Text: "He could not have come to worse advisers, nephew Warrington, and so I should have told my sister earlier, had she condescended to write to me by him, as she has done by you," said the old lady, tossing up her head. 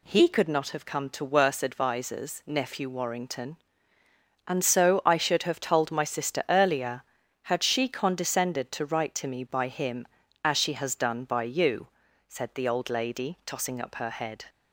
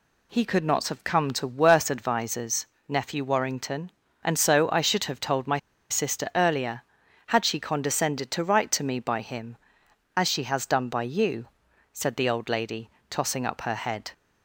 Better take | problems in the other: first | pauses between "my" and "sister"; slight; at 5.5 s; 0.32 s long

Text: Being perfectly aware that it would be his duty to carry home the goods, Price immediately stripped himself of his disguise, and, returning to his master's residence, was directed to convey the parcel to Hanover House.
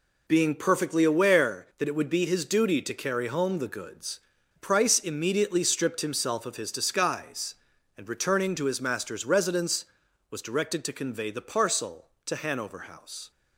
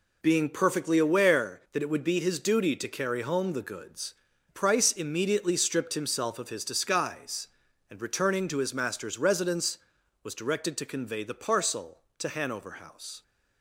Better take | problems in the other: neither | none

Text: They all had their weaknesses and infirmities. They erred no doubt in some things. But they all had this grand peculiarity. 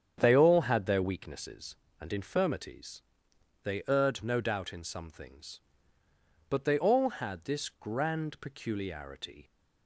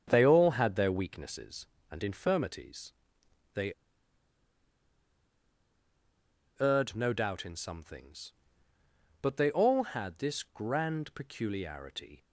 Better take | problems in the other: first | starts louder than the rest; strong; until 1.0 s; 8 dB; strong in the first // pauses between "They" and "erred"; strong; at 3.7 s; 2.8 s long

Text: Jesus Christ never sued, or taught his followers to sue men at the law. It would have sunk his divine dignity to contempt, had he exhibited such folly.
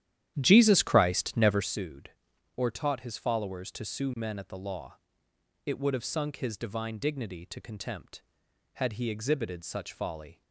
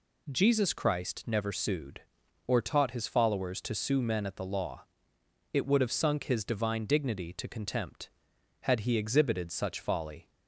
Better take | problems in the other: second | starts louder than the rest; strong; until 1.7 s; 11.5 dB

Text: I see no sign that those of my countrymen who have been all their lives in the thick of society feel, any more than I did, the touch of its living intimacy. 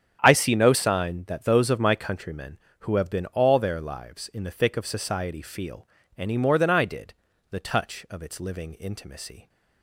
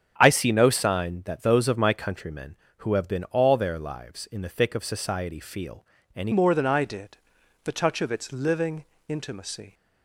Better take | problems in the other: first | starts louder than the rest; strong; until 1.1 s; 7.5 dB; strong in the first // changes voice at "more"; from 6.3 s on; 3.4 s long // pauses between "living" and "intimacy"; slight; at 8.8 s; 0.24 s long

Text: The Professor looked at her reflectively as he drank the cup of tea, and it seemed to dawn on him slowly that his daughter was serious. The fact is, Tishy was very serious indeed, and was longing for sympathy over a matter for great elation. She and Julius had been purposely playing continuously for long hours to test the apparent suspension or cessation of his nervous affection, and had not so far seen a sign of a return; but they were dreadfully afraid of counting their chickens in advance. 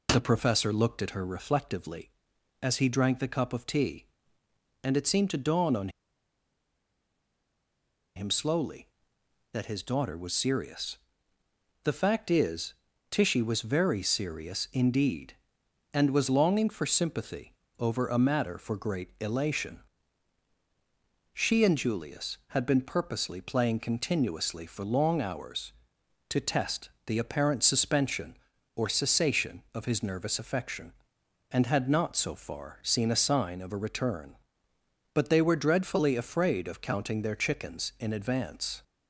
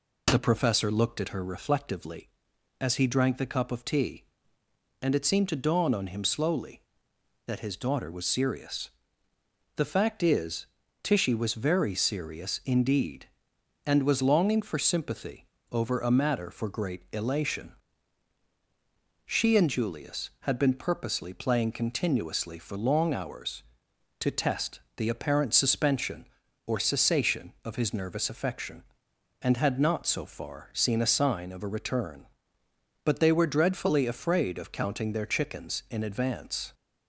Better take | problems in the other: second | pauses between "on" and "him"; strong; at 5.8 s; 2.2 s long // pauses between "sympathy" and "over"; slight; at 17.5 s; 0.26 s long; slight in the second // pauses between "test" and "the"; slight; at 26.8 s; 0.18 s long; slight in the second

